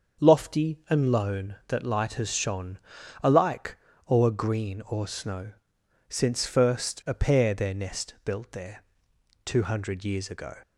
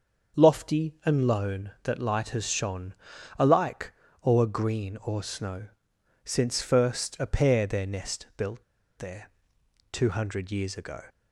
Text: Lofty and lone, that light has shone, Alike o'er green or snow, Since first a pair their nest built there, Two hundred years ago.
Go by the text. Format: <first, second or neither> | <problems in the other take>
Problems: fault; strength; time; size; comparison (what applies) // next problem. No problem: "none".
first | starts louder than the rest; until 1.4 s; 6.5 dB; also in the first // pauses between "Alike" and "o'er"; slight; at 3.9 s; 0.34 s long; slight in the first // pauses between "built" and "there"; slight; at 8.6 s; 0.34 s long